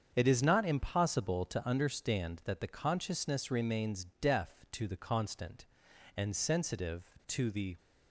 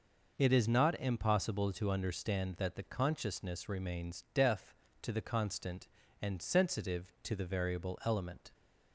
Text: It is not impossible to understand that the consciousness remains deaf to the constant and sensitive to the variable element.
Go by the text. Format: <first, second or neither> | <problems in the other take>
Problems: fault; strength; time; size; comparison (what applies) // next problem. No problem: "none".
second | starts louder than the rest; strong; until 1.1 s; 7 dB // pauses between "remains" and "deaf"; slight; at 4.0 s; 0.16 s long // stops before "variable element"; at 7.7 s